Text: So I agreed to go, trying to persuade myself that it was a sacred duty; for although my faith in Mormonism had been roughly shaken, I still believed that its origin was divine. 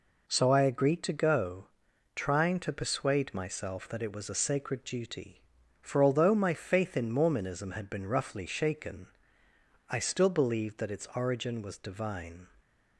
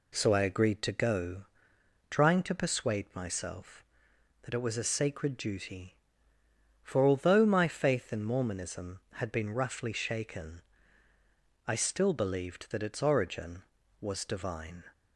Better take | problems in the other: neither | none

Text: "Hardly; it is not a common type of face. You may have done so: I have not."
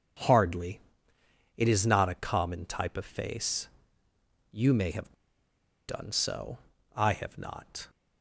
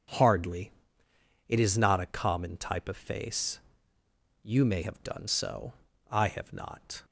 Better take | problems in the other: second | pauses between "have" and "done"; noticeable; at 5.1 s; 0.74 s long

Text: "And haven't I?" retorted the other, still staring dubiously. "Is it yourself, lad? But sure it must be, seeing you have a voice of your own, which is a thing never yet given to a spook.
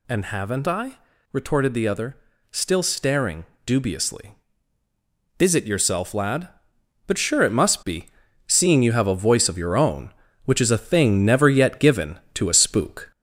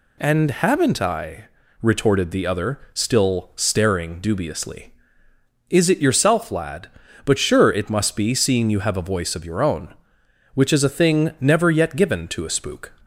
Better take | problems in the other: second | gets louder; slight; throughout; 3 dB // pauses between "staring" and "dubiously"; slight; at 3.4 s; 0.18 s long

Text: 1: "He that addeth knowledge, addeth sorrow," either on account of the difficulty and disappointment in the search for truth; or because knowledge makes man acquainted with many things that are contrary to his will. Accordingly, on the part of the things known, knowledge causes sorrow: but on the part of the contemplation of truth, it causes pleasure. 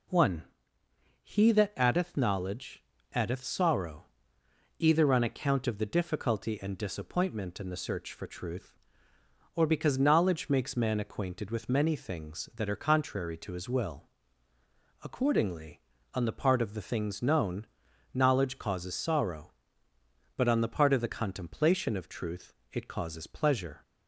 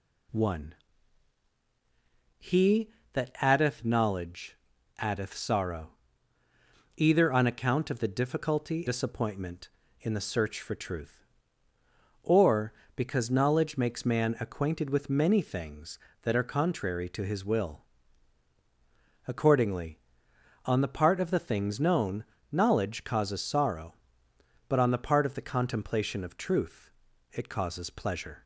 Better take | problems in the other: first | skips "and"; at 8.8 s

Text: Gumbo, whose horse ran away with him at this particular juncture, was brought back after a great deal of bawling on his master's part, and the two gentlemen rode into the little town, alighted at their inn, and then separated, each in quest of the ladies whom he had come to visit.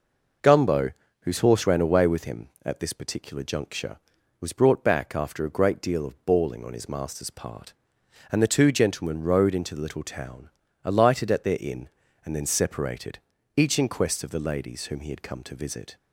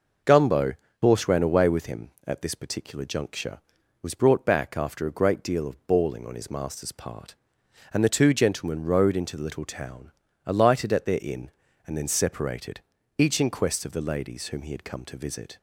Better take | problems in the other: first | skips "whose"; at 0.8 s

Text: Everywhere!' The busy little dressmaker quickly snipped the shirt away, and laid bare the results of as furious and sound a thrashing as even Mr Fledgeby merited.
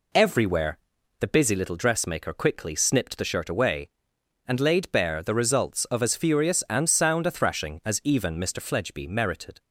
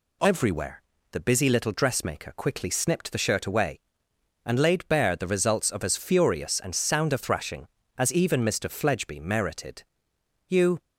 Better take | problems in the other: first | goes on to say "You"; slight; from 10.4 s on; 0.32 s long

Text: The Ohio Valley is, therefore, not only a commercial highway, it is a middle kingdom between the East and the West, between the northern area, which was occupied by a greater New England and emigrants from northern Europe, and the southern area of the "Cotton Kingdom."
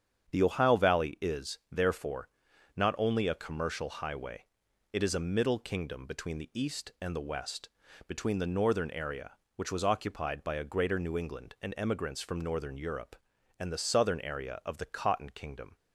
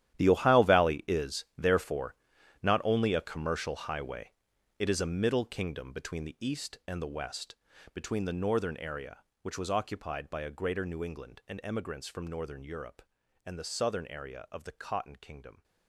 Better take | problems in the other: first | gets quieter; strong; throughout; 14.5 dB // starts louder than the rest; strong; until 1.2 s; 11.5 dB; strong in the first

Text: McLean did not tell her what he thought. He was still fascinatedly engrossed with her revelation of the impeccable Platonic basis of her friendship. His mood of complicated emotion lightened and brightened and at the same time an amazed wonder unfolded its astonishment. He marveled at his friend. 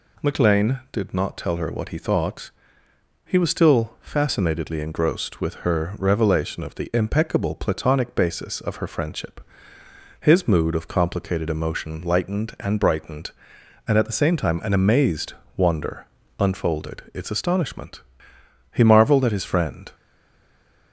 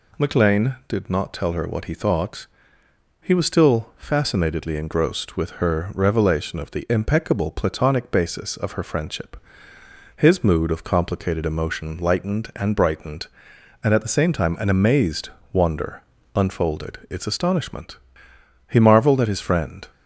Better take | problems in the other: second | pauses between "amazed" and "wonder"; slight; at 15.3 s; 0.22 s long; slight in the second // pauses between "wonder" and "unfolded"; slight; at 16.0 s; 0.32 s long; slight in the second // stays silent after the last word; slight; from 19.9 s on; 1.0 s long

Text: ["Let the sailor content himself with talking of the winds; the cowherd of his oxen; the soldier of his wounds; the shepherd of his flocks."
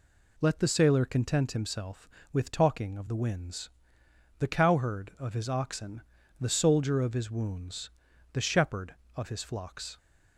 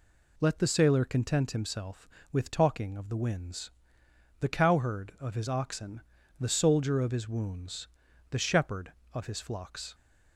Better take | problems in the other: neither | none

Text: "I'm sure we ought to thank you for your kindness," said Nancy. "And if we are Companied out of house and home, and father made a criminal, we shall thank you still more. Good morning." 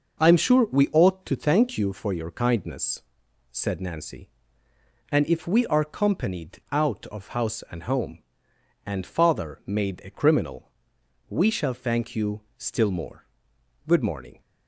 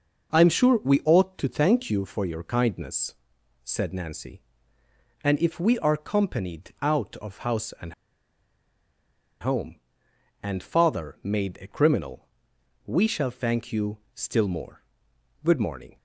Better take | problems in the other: first | pauses between "and" and "home"; strong; at 7.9 s; 1.4 s long // pauses between "you" and "still"; slight; at 13.9 s; 0.16 s long; slight in the first

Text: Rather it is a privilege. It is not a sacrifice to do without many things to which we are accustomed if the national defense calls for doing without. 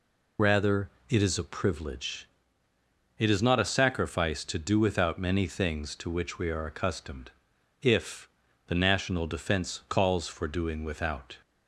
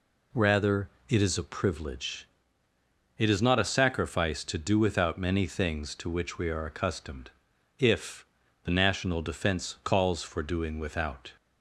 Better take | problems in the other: second | loses the start of "Rather"; at 0.3 s; 65 ms // pauses between "Rather" and "it"; slight; at 0.8 s; 0.20 s long; slight in the second // pauses between "accustomed" and "if"; noticeable; at 7.3 s; 0.50 s long; noticeable in the second // pauses between "if" and "the"; at 8.2 s; 0.40 s long; also in the second

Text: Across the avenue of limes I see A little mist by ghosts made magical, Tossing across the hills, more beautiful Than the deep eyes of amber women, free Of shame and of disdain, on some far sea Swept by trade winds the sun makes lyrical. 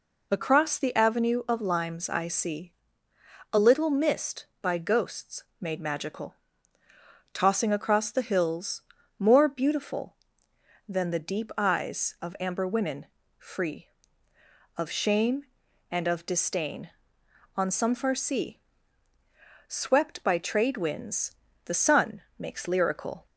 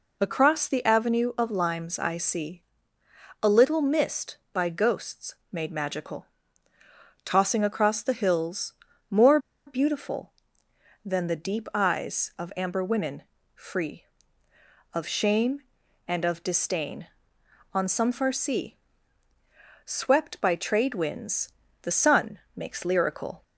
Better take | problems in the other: first | pauses between "see" and "A"; noticeable; at 2.6 s; 0.80 s long; noticeable in the first // pauses between "ghosts" and "made"; slight; at 5.3 s; 0.18 s long; slight in the first // pauses between "more" and "beautiful"; slight; at 9.3 s; 0.27 s long // pauses between "sea" and "Swept"; at 18.7 s; 1.0 s long; also in the first // pauses between "winds" and "the"; slight; at 21.5 s; 0.30 s long; slight in the first // pauses between "sun" and "makes"; slight; at 22.3 s; 0.16 s long; slight in the first

